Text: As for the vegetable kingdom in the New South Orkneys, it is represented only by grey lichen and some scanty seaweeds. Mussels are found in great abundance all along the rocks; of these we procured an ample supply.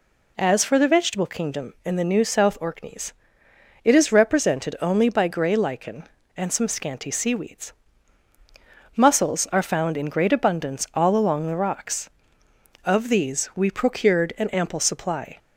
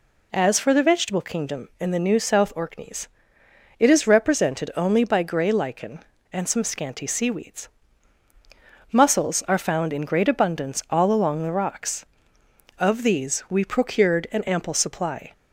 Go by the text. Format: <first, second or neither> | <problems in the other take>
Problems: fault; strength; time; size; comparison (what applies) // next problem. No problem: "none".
neither | none